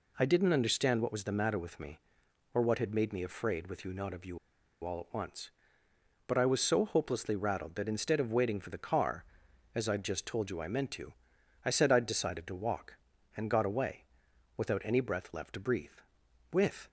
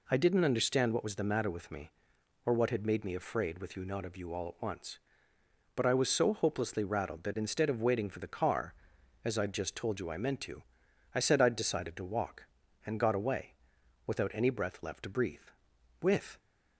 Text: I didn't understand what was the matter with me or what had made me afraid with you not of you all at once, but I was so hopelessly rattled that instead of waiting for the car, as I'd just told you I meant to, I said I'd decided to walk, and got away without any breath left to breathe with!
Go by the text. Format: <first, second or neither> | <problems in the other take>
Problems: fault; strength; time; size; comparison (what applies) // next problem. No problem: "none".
second | pauses between "you" and "all"; noticeable; at 4.3 s; 0.46 s long // pauses between "away" and "without"; noticeable; at 14.0 s; 0.54 s long; noticeable in the second